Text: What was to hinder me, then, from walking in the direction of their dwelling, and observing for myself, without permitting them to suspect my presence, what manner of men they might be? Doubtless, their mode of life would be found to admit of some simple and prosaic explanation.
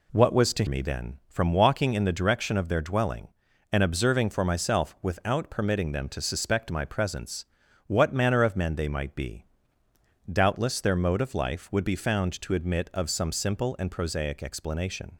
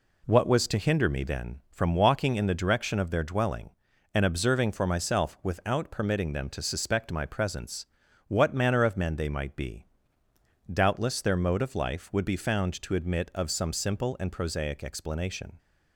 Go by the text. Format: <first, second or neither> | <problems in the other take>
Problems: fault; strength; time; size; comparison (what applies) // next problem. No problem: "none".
second | skips "hinder"; at 0.6 s